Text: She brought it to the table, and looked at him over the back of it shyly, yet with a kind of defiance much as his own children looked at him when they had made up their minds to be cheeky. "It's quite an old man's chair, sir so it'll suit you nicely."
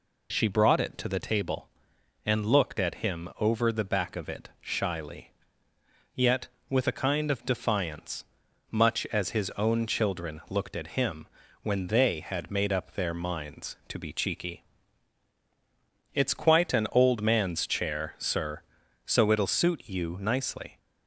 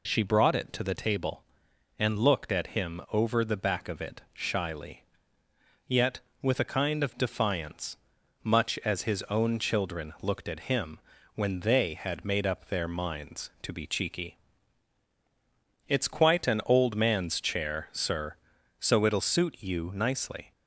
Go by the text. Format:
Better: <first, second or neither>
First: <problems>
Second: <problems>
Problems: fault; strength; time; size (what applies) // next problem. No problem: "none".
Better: neither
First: pauses between "defiance" and "much"; noticeable; at 8.2 s; 0.48 s long // pauses between "him" and "when"; slight; at 11.2 s; 0.36 s long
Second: pauses between "defiance" and "much"; noticeable; at 7.9 s; 0.48 s long // pauses between "him" and "when"; slight; at 10.9 s; 0.36 s long